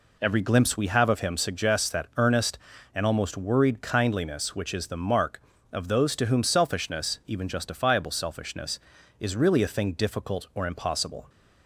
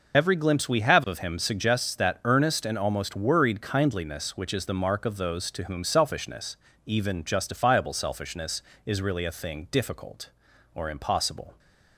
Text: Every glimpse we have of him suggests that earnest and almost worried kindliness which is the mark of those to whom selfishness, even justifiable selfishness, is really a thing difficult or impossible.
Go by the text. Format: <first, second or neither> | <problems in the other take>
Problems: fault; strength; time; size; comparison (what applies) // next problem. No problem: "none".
first | loses the start of "Every"; at 0.1 s; 25 ms